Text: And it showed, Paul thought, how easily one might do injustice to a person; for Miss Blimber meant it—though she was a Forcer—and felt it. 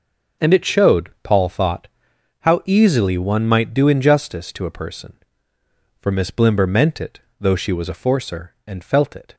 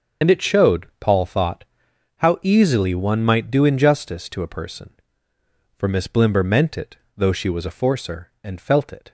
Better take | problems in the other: first | loses the start of "And"; at 0.2 s; 40 ms // starts louder than the rest; until 1.3 s; 6.5 dB; noticeable in the first

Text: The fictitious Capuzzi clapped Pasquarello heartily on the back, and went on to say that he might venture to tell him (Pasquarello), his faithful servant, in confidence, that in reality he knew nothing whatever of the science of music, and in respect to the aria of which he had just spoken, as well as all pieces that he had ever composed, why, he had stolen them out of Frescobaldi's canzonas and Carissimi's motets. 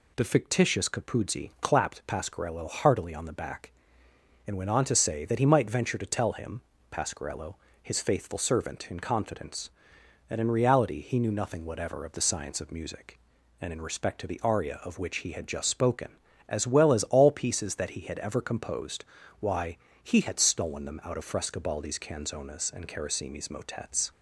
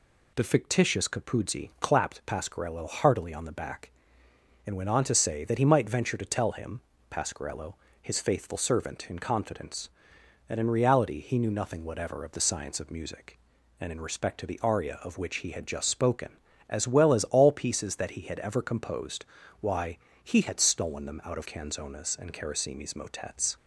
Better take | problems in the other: first | skips "Frescobaldi's"; at 21.4 s

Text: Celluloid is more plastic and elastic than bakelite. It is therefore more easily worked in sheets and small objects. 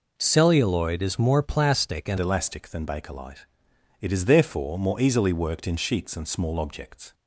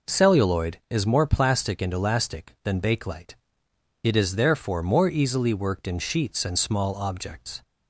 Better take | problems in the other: second | changes voice at "elastic"; from 2.1 s on; 5.0 s long

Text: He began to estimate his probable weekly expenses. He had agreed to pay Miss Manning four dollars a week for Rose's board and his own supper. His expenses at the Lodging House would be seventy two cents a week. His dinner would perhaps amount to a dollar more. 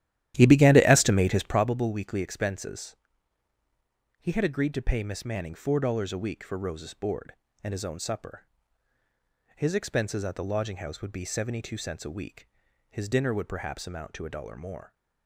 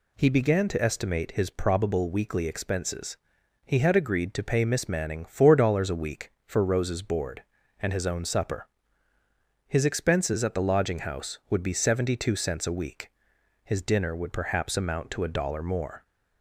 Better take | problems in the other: second | starts louder than the rest; strong; until 1.6 s; 12.5 dB

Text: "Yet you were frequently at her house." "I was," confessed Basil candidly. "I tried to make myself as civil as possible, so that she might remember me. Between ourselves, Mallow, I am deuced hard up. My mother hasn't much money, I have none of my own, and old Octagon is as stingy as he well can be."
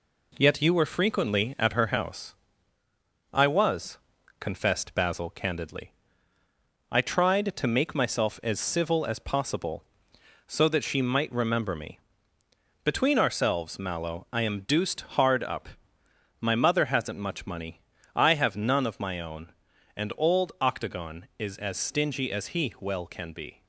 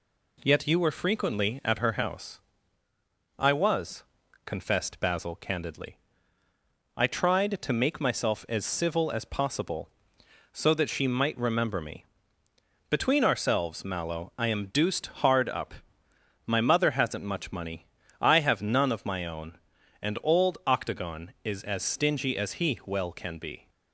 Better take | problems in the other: second | gets quieter; noticeable; throughout; 4 dB

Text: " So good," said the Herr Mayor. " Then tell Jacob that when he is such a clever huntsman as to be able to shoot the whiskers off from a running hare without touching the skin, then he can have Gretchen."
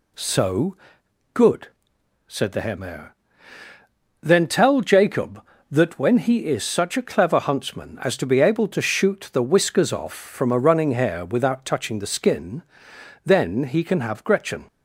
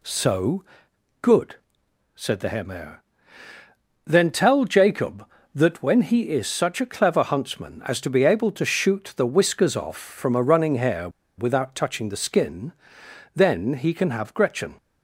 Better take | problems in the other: first | pauses between "So" and "good"; noticeable; at 0.6 s; 0.56 s long; noticeable in the first // pauses between "hare" and "without"; slight; at 11.0 s; 0.29 s long

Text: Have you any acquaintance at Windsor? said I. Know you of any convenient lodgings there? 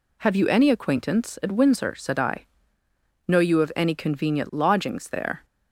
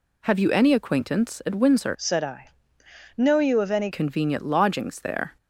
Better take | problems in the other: first | changes voice from "said" to "any"; from 1.9 to 3.9 s; 2.0 s long

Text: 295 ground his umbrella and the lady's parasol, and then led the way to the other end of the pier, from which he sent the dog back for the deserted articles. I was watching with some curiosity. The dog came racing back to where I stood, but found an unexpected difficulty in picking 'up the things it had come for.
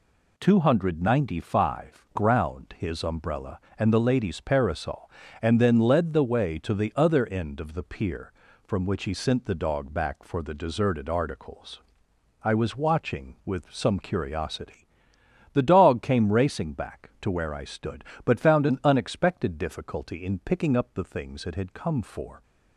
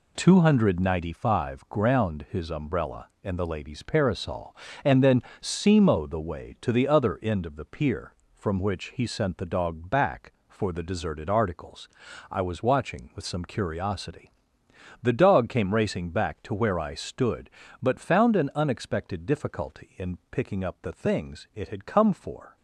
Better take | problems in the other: first | says "simo" for "led"; at 5.4 s

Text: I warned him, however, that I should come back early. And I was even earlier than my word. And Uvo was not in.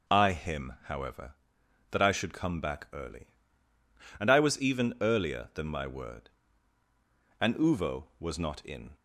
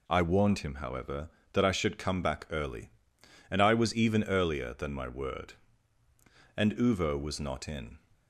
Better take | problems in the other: second | skips "warned"; at 0.3 s

